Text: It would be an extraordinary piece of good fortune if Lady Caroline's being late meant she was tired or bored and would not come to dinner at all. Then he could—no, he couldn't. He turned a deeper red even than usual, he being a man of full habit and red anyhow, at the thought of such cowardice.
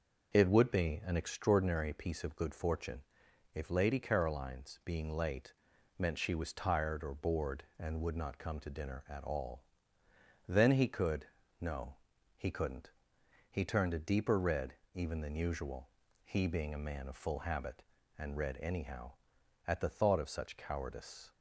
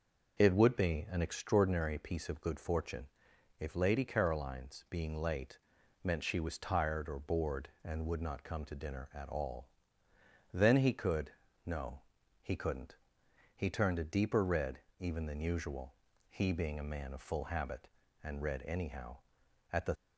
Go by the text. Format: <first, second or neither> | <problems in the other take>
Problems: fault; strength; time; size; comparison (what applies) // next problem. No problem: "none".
first | pauses between "fortune" and "if"; noticeable; at 3.0 s; 0.52 s long; noticeable in the first // pauses between "late" and "meant"; noticeable; at 5.5 s; 0.46 s long; noticeable in the first // pauses between "red" and "even"; slight; at 14.7 s; 0.20 s long; slight in the first // stops before "thought of such cowardice"; at 19.9 s